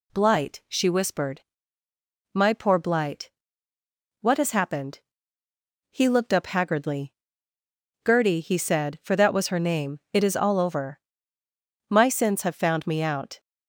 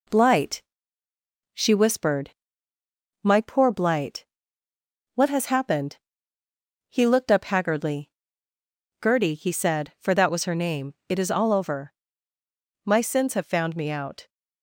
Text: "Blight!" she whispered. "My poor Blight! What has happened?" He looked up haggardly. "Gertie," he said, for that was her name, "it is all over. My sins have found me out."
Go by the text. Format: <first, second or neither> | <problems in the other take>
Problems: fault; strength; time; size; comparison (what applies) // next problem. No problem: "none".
first | gets quieter; slight; throughout; 2.5 dB